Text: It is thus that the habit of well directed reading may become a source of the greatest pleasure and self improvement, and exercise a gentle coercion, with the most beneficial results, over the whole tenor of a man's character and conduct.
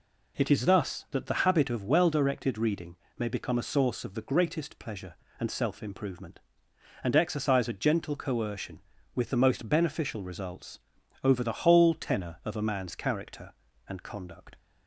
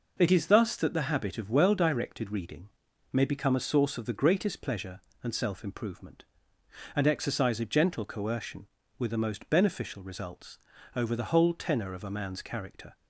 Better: first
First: pauses between "reading" and "may"; slight; at 2.9 s; 0.22 s long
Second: pauses between "reading" and "may"; at 2.6 s; 0.44 s long // stops before "and conduct"; at 12.9 s

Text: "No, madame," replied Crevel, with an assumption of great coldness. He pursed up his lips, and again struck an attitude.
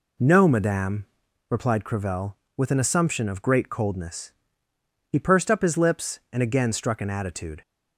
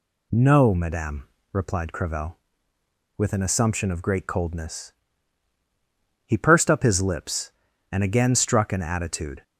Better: neither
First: none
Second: none

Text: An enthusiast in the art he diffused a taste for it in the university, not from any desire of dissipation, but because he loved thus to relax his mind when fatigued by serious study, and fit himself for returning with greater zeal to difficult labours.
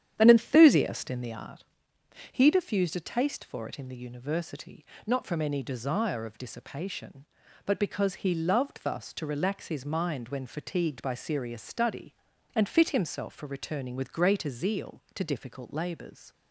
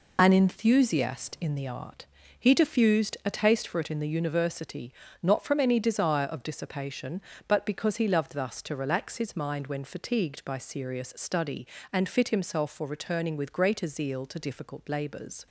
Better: second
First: starts louder than the rest; strong; until 1.4 s; 9.5 dB // pauses between "art" and "he"; noticeable; at 1.6 s; 0.68 s long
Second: pauses between "art" and "he"; slight; at 2.0 s; 0.34 s long

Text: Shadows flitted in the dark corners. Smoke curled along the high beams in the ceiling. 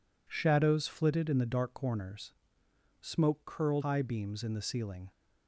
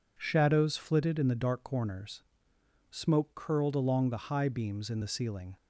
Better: second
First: skips "along the"; at 3.8 s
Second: none

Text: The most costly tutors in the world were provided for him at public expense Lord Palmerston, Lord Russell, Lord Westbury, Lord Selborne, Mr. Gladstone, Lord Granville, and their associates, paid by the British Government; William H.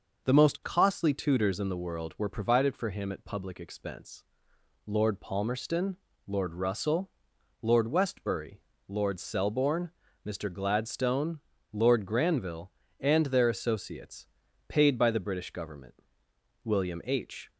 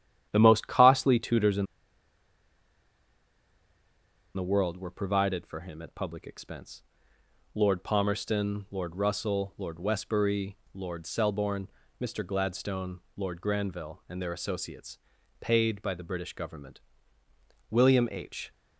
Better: first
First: pauses between "expense" and "Lord"; noticeable; at 4.2 s; 0.62 s long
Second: starts louder than the rest; strong; until 1.3 s; 10.5 dB // pauses between "in" and "the"; strong; at 1.6 s; 2.6 s long // pauses between "expense" and "Lord"; noticeable; at 6.8 s; 0.72 s long

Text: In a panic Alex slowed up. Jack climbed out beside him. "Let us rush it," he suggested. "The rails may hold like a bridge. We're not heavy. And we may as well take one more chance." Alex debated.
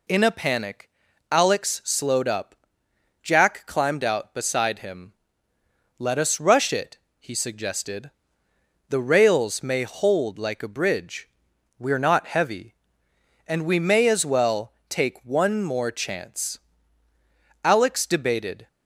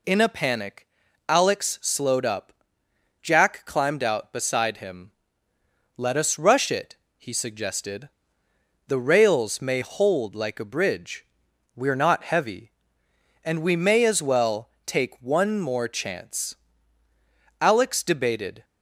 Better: neither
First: pauses between "panic" and "Alex"; at 0.8 s; 0.42 s long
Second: pauses between "panic" and "Alex"; at 0.8 s; 0.42 s long

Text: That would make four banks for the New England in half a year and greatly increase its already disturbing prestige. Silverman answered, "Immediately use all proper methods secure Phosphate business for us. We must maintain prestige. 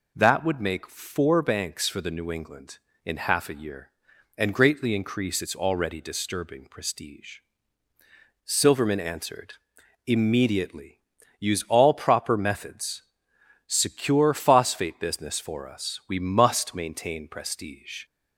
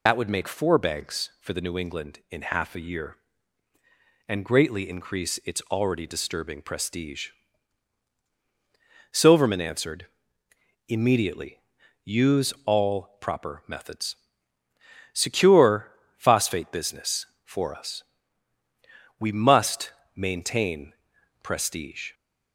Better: first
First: pauses between "Immediately" and "use"; at 10.9 s; 0.40 s long // pauses between "methods" and "secure"; noticeable; at 13.0 s; 0.64 s long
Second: loses the start of "That"; at 0.0 s; 60 ms // pauses between "Immediately" and "use"; at 11.5 s; 0.44 s long // pauses between "methods" and "secure"; noticeable; at 14.1 s; 0.98 s long // pauses between "secure" and "Phosphate"; slight; at 15.9 s; 0.24 s long // pauses between "must" and "maintain"; slight; at 19.9 s; 0.24 s long // pauses between "maintain" and "prestige"; noticeable; at 20.9 s; 0.50 s long

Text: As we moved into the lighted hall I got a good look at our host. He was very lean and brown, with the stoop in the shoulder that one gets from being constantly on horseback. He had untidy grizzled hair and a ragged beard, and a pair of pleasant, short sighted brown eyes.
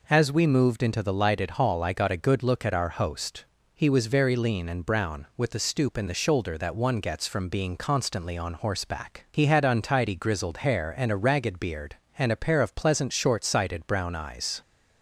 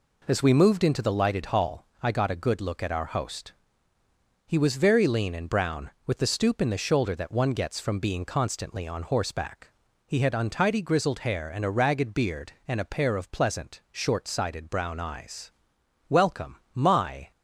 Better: first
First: none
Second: pauses between "hall" and "I"; slight; at 1.8 s; 0.16 s long // goes on to say "Welcome my"; noticeable; from 16.0 s on; 1.2 s long

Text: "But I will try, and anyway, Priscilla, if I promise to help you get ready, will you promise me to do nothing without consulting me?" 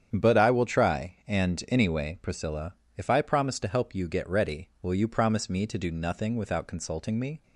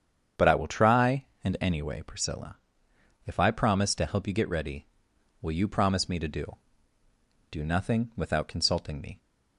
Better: first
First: starts louder than the rest; strong; until 1.1 s; 8.5 dB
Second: starts louder than the rest; strong; until 1.5 s; 8 dB // says "do" twice; at 7.4 s

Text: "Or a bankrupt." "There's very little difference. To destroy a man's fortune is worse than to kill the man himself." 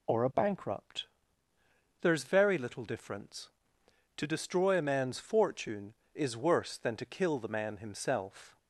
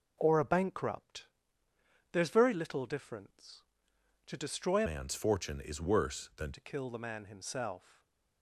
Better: first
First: none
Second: changes voice from "man's" to "than"; from 4.8 to 6.5 s; 1.7 s long // stays silent after the last word; slight; from 7.9 s on; 0.5 s long

